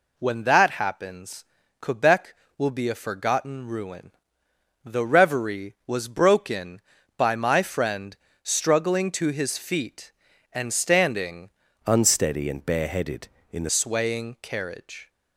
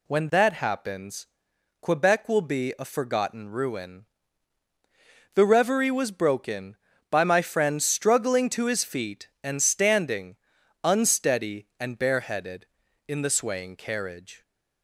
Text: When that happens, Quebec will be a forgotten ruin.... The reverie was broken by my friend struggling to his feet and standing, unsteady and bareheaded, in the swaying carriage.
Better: second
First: pauses between "friend" and "struggling"; slight; at 8.1 s; 0.30 s long // changes voice from "unsteady" to "the"; from 11.8 to 13.6 s; 1.8 s long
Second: none

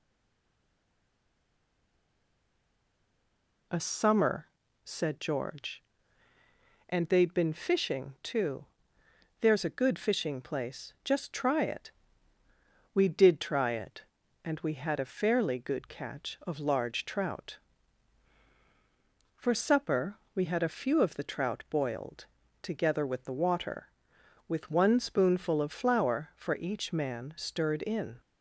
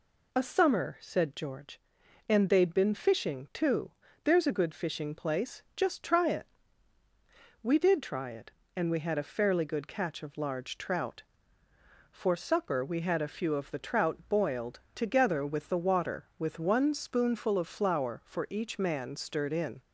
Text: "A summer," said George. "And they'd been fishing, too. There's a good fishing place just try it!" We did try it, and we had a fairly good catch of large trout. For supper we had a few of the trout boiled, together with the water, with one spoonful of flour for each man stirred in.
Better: second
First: stays silent before the first word; strong; until 3.6 s; 3.6 s long // pauses between "supper" and "we"; slight; at 20.1 s; 0.20 s long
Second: none

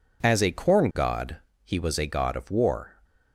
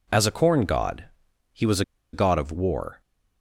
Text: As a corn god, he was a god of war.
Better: first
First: none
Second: pauses between "was" and "a"; slight; at 1.8 s; 0.31 s long

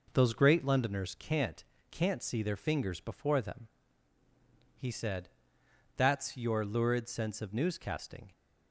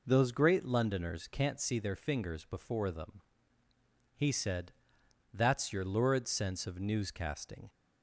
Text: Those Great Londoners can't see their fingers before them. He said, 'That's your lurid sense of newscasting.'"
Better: second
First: says "can't" twice; at 1.9 s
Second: none

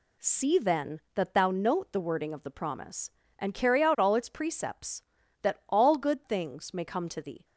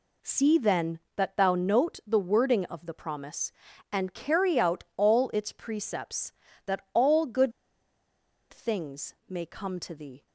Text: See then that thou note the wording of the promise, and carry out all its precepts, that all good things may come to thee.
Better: first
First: none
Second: pauses between "good" and "things"; at 7.5 s; 1.0 s long

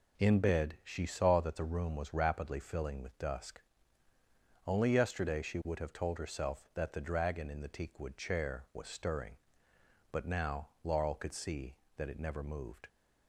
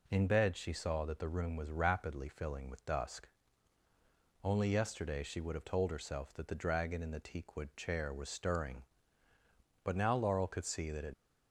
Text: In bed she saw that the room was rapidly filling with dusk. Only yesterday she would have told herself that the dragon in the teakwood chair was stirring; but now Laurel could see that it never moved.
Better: first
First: none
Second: stops before "never moved"; at 11.1 s

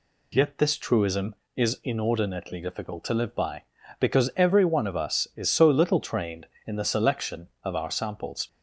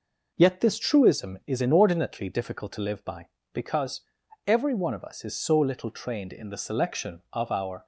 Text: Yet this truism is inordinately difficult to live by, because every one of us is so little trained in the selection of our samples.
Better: first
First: none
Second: pauses between "because" and "every"; noticeable; at 4.0 s; 0.46 s long // stops before "samples"; at 7.8 s

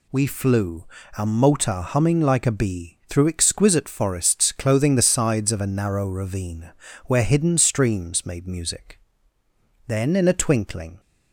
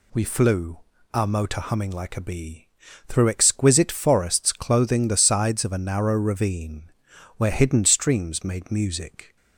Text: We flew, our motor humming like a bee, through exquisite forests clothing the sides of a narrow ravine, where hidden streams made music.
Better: second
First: goes on to say "Then in a twinkling"; noticeable; from 9.8 s on; 1.1 s long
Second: none

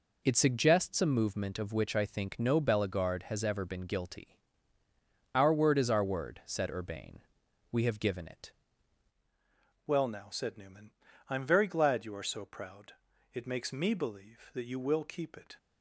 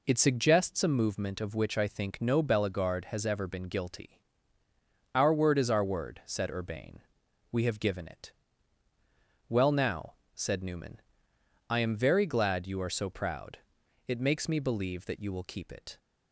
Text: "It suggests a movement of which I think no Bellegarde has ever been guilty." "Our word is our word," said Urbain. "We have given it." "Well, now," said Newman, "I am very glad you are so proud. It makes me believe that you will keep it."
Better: second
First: changes voice at "Well"; from 9.8 s on; 5.7 s long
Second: none

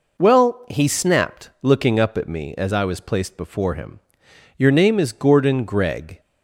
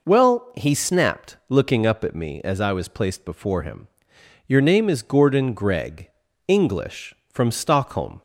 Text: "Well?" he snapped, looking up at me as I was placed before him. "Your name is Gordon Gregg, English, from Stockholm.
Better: second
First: stops before "English from Stockholm"; at 6.1 s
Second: none

